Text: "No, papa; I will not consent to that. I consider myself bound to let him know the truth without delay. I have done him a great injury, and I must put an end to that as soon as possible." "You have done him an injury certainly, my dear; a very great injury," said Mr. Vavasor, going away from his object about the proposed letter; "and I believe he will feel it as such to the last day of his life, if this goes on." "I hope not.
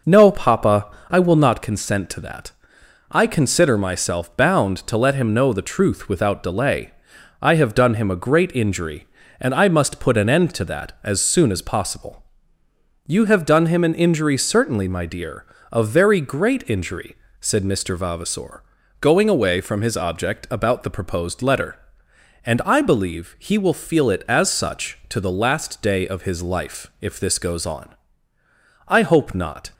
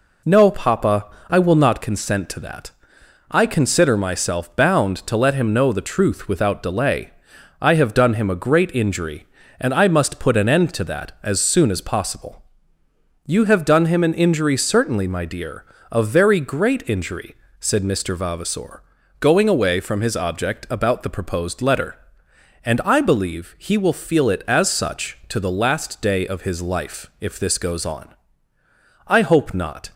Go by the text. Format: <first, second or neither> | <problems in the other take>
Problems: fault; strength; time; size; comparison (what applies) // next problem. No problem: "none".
second | starts louder than the rest; noticeable; until 1.0 s; 5.5 dB